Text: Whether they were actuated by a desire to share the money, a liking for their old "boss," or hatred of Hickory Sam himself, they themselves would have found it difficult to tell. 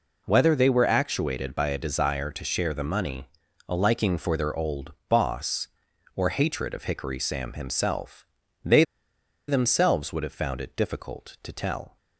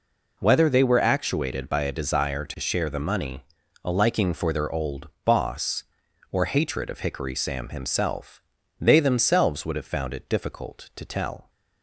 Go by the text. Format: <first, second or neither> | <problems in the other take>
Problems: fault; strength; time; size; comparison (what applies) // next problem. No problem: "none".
second | pauses between "old" and "boss"; slight; at 4.9 s; 0.16 s long; slight in the second // pauses between "they" and "themselves"; noticeable; at 8.8 s; 0.64 s long